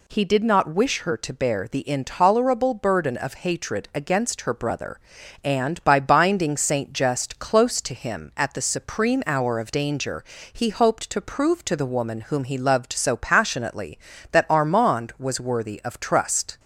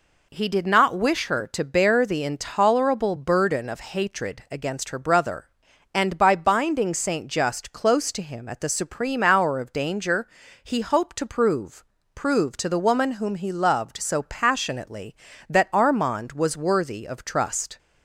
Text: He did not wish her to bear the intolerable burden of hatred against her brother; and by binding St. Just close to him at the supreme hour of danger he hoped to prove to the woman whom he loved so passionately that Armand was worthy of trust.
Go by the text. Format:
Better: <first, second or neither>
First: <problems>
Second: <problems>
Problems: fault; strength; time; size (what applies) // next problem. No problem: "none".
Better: first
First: pauses between "danger" and "he"; slight; at 10.2 s; 0.30 s long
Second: pauses between "danger" and "he"; at 10.2 s; 0.38 s long // says "prove" twice; at 12.1 s